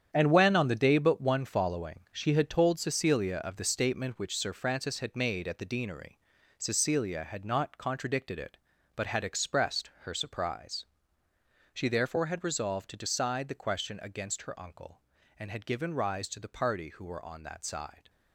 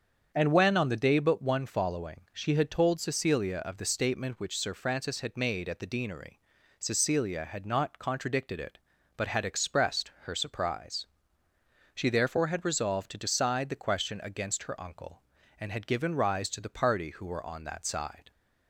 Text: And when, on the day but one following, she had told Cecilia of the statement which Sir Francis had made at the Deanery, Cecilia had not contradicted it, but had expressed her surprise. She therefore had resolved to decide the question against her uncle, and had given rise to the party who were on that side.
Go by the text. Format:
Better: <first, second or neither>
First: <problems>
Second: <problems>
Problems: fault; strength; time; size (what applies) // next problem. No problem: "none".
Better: second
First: gets quieter; strong; throughout; 10.5 dB // starts louder than the rest; strong; until 1.1 s; 9 dB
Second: starts louder than the rest; strong; until 1.3 s; 7.5 dB